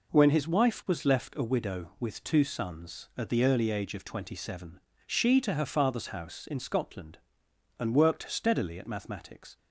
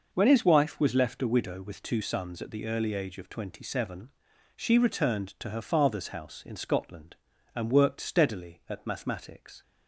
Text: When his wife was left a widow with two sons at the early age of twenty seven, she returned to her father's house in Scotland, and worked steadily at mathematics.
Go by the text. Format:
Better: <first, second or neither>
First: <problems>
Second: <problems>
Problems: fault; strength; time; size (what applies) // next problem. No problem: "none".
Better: second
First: skips "returned"; at 5.4 s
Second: none